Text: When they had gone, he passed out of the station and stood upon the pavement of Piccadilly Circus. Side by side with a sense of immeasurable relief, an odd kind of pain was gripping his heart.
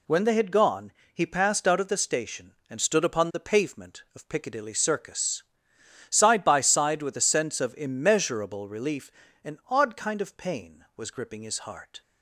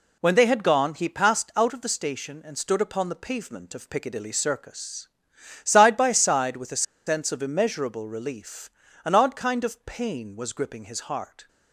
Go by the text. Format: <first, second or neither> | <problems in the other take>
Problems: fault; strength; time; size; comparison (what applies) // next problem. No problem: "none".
first | pauses between "a" and "sense"; slight; at 6.8 s; 0.24 s long